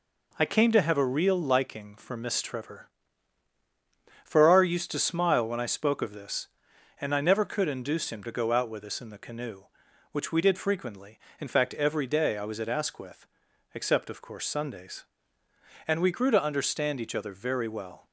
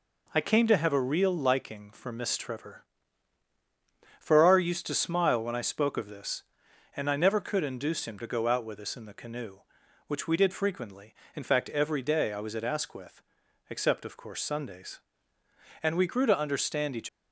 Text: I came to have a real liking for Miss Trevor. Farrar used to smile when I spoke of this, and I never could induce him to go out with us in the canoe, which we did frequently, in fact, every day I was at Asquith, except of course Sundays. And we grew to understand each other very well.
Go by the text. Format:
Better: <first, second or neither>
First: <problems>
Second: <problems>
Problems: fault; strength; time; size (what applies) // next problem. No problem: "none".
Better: first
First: none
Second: stops before "other very well"; at 17.0 s